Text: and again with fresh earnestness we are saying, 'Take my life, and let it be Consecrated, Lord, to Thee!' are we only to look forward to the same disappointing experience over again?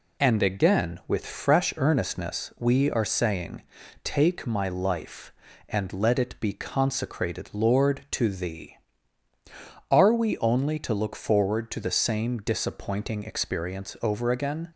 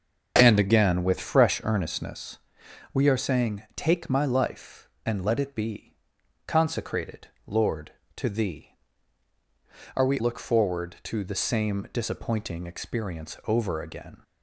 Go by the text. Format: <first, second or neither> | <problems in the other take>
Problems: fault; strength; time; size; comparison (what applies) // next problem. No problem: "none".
first | starts louder than the rest; until 1.3 s; 6 dB // pauses between "earnestness" and "we"; noticeable; at 2.3 s; 0.56 s long // pauses between "be" and "Consecrated"; noticeable; at 5.9 s; 0.50 s long // skips "only to"; at 10.2 s